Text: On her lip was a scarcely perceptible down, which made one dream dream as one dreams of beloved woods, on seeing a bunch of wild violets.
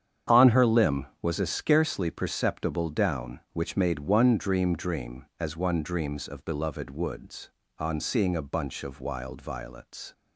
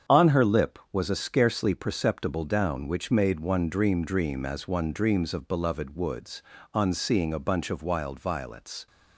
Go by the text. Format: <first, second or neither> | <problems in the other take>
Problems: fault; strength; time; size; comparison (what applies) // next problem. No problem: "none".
second | starts louder than the rest; strong; until 1.4 s; 8.5 dB; strong in the second // says "limb" for "lip"; at 0.6 s